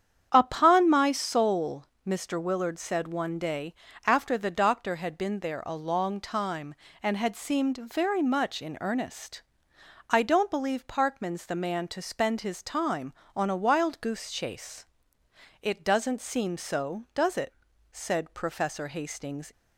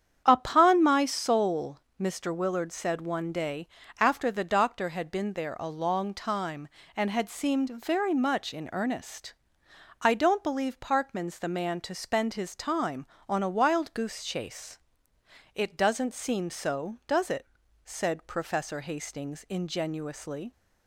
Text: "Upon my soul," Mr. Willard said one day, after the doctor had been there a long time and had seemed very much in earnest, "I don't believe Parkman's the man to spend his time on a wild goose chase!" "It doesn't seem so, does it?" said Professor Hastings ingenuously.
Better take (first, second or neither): second